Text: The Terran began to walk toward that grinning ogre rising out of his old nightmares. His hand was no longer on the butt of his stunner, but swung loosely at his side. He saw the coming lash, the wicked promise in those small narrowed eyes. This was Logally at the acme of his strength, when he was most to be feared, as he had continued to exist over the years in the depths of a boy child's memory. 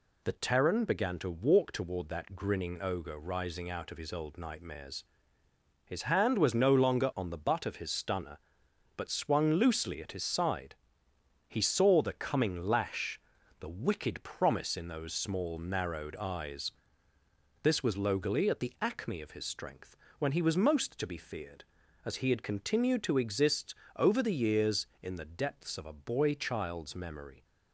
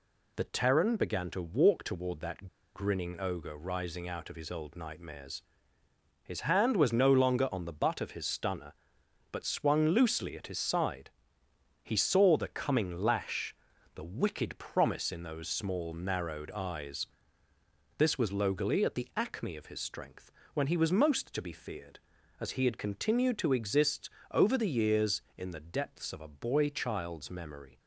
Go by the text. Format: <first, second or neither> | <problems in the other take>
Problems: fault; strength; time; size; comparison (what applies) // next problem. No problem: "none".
first | pauses between "that" and "grinning"; slight; at 2.4 s; 0.28 s long // pauses between "exist" and "over"; slight; at 24.1 s; 0.20 s long; slight in the first